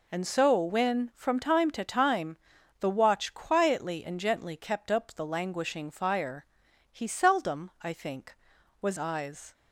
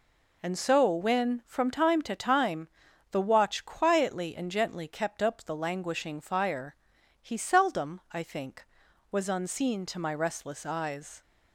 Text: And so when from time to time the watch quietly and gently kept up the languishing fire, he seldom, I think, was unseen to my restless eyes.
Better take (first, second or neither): second